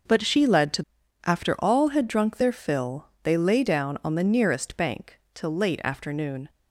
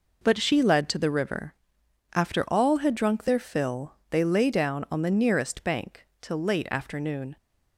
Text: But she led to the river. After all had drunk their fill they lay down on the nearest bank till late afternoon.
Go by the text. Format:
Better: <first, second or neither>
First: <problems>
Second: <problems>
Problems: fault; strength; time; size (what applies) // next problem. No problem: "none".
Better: second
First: skips "the river"; at 1.0 s // pauses between "fill" and "they"; slight; at 3.0 s; 0.16 s long // pauses between "bank" and "till"; slight; at 5.1 s; 0.16 s long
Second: pauses between "fill" and "they"; slight; at 3.9 s; 0.16 s long // pauses between "bank" and "till"; slight; at 6.0 s; 0.16 s long